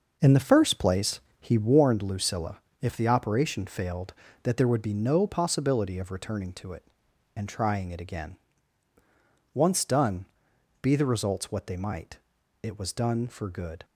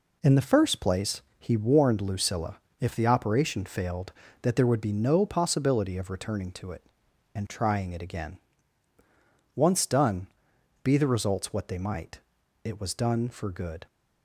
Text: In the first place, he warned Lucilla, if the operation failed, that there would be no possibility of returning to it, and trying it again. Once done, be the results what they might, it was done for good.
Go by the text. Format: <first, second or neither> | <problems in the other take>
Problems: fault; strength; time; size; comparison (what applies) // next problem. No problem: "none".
second | starts louder than the rest; noticeable; until 2.0 s; 5.5 dB